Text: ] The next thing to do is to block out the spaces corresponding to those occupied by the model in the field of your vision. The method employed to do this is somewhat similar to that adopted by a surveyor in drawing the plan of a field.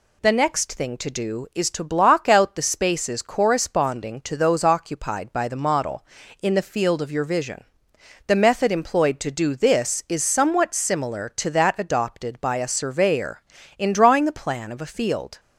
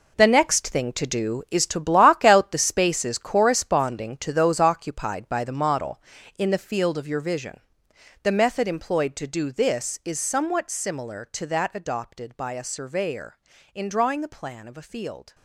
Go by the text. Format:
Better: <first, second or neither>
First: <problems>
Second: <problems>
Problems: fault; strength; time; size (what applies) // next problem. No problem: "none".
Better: first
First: none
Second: gets quieter; strong; throughout; 11 dB